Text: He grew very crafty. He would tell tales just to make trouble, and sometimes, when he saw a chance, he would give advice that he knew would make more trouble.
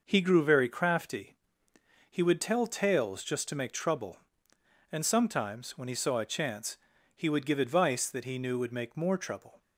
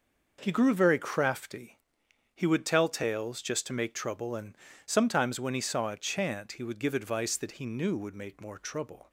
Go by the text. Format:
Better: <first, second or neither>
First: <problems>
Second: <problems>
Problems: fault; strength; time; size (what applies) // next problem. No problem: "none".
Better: first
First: none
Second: pauses between "and" and "sometimes"; slight; at 4.5 s; 0.30 s long // says "chant" for "chance"; at 5.9 s